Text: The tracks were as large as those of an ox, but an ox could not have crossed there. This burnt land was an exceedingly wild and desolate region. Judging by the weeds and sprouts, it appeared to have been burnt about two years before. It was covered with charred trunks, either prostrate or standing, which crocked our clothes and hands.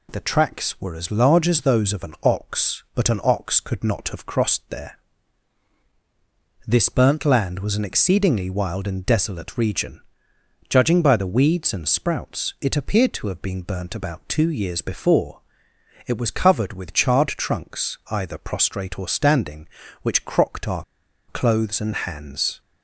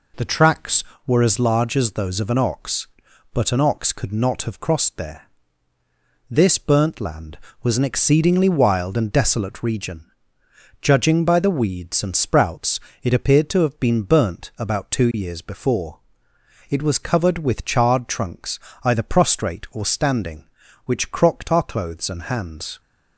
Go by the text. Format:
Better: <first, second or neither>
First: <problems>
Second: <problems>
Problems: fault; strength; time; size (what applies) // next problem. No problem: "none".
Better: second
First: pauses between "our" and "clothes"; at 20.8 s; 0.44 s long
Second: none